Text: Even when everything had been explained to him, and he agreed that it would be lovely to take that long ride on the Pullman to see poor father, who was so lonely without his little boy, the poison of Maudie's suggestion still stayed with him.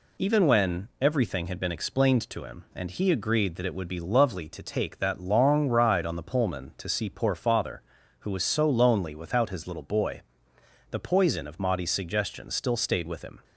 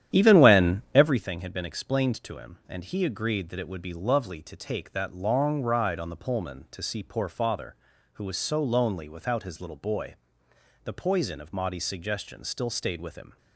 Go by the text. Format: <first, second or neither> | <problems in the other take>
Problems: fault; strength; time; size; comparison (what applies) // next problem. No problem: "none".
first | starts louder than the rest; strong; until 1.2 s; 10.5 dB